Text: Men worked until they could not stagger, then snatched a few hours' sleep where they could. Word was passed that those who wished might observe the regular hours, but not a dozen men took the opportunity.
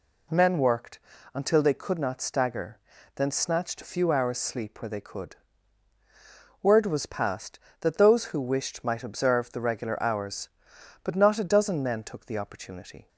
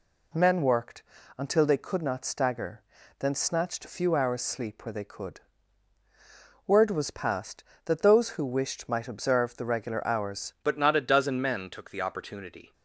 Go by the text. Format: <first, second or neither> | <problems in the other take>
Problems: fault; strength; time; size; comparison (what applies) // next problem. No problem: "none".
first | pauses between "worked" and "until"; slight; at 1.0 s; 0.34 s long; slight in the first // changes voice at "but"; from 10.6 s on; 2.1 s long